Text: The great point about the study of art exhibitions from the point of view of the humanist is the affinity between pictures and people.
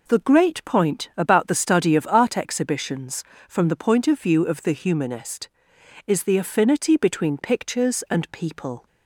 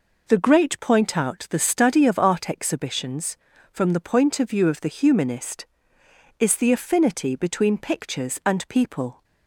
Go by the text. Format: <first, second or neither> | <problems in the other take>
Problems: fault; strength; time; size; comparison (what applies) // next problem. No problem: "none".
first | says "out" for "about"; at 1.1 s